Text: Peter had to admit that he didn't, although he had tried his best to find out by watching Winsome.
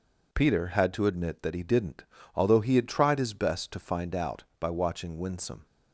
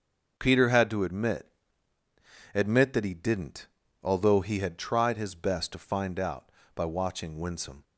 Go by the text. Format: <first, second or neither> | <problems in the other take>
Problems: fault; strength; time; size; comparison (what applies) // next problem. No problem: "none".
first | starts louder than the rest; noticeable; until 1.3 s; 6 dB // says "admit" twice; at 2.5 s